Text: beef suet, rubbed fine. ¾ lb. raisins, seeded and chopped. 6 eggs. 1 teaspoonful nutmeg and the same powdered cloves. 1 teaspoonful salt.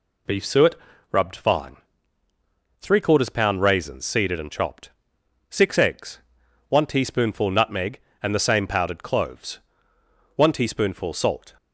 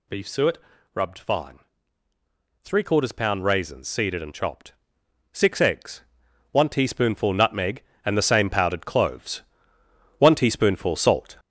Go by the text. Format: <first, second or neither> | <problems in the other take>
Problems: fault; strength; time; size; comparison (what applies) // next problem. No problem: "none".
first | gets louder; noticeable; throughout; 5 dB